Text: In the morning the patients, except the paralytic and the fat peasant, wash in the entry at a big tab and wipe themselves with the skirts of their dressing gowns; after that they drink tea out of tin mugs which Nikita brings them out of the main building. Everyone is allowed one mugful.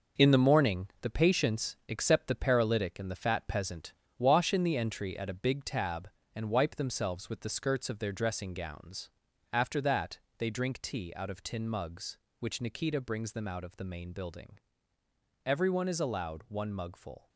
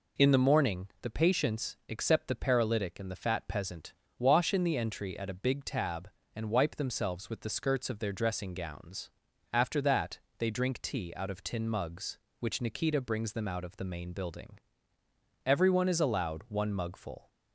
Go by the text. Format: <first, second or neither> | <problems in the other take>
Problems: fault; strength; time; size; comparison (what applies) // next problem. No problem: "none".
second | gets quieter; strong; throughout; 8.5 dB // pauses between "morning" and "the"; slight; at 0.8 s; 0.16 s long; slight in the second // pauses between "that" and "they"; slight; at 10.1 s; 0.22 s long; slight in the second